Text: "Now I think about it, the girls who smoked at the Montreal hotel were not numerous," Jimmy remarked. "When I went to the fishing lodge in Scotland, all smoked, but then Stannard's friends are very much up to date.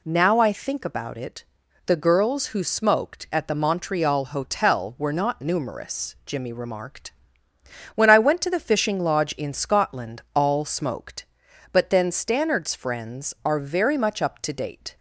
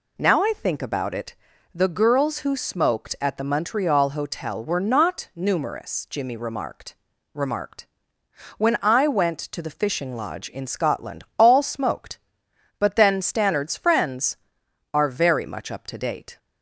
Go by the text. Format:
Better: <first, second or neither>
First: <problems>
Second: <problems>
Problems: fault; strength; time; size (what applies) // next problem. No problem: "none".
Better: first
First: none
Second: says "remarked" twice; at 7.3 s